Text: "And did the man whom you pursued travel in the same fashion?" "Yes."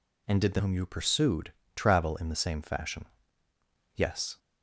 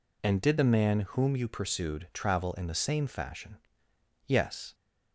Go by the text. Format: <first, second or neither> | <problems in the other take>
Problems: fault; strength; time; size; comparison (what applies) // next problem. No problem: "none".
second | skips "man"; at 0.5 s // pauses between "pursued" and "travel"; slight; at 1.5 s; 0.22 s long